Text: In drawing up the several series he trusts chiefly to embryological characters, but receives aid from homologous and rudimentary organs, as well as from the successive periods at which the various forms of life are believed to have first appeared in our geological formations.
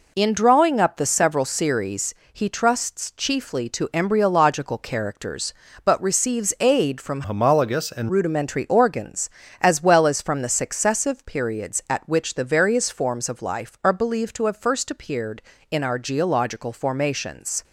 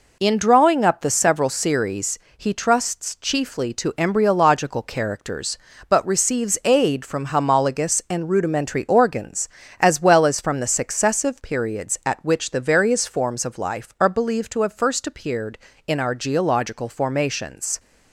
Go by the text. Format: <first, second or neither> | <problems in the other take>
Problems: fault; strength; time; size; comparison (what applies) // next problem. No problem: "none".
second | pauses between "series" and "he"; slight; at 2.1 s; 0.18 s long; slight in the second // changes voice from "homologous" to "and"; from 7.2 to 8.0 s; 0.8 s long